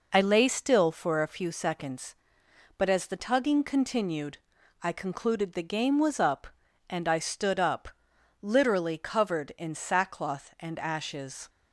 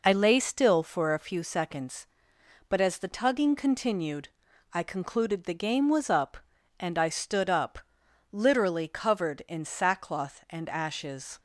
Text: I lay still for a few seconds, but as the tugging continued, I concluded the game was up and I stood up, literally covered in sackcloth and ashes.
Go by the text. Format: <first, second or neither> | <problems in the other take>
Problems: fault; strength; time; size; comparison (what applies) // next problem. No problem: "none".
neither | none